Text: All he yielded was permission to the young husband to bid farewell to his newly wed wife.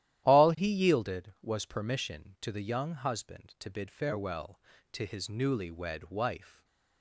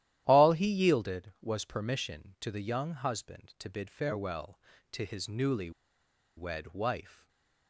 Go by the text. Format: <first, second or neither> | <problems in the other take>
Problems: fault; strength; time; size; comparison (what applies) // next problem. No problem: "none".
first | starts louder than the rest; strong; until 1.2 s; 12.5 dB; strong in the first // pauses between "newly" and "wed"; noticeable; at 5.6 s; 0.66 s long // stays silent after the last word; slight; from 7.1 s on; 0.5 s long